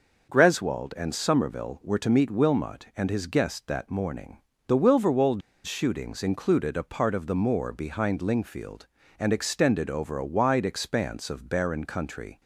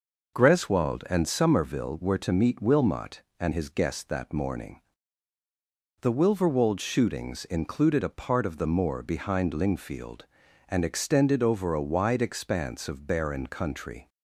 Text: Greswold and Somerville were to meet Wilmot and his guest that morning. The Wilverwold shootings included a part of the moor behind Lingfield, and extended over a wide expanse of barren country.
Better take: second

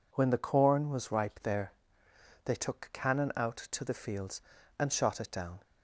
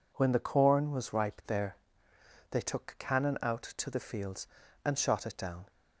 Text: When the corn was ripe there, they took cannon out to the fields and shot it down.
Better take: neither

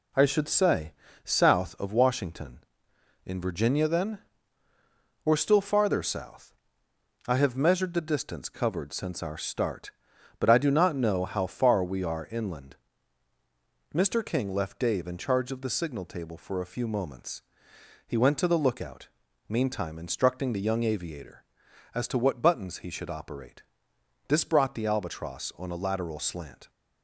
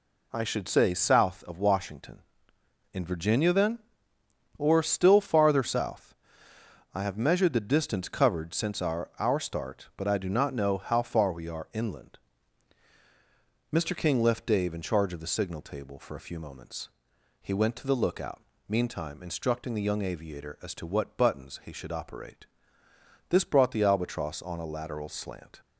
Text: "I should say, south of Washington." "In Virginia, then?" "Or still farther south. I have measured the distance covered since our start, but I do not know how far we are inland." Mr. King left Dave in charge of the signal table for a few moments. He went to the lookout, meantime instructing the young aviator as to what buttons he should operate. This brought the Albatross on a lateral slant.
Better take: first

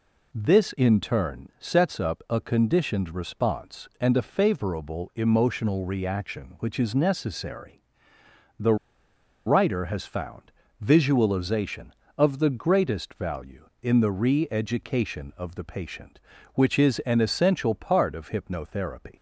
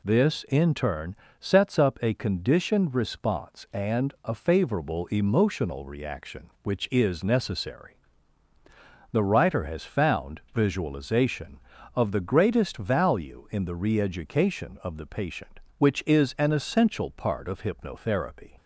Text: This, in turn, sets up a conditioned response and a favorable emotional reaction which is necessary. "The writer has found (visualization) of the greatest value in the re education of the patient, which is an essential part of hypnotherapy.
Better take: second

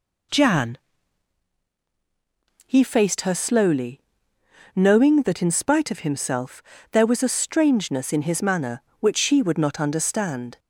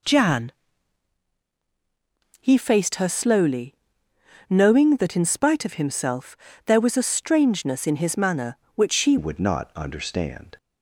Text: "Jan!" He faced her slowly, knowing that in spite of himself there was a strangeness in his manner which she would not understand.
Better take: first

